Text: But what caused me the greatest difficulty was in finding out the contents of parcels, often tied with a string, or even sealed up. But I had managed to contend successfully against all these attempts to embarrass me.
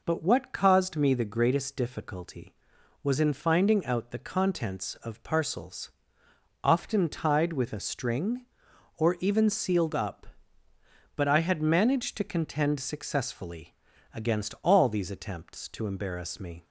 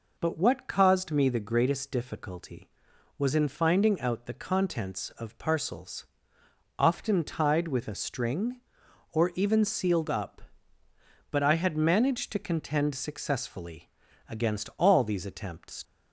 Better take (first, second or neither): first